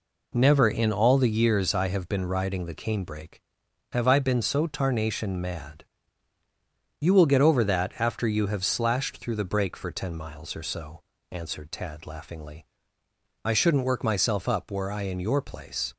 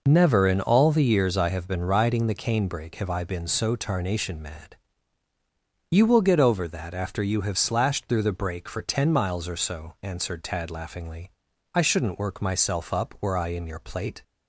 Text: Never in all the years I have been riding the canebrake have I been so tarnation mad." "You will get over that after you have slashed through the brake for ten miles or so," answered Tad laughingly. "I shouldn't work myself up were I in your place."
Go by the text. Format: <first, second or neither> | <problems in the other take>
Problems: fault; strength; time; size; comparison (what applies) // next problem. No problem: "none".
first | says "plate" for "place"; at 13.7 s